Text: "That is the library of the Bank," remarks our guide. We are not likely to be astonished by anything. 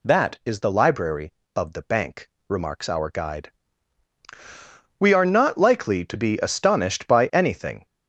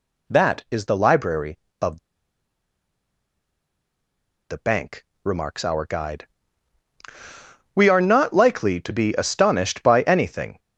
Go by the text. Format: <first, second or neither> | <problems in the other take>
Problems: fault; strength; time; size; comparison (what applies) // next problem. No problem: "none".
first | pauses between "of" and "the"; strong; at 1.9 s; 2.5 s long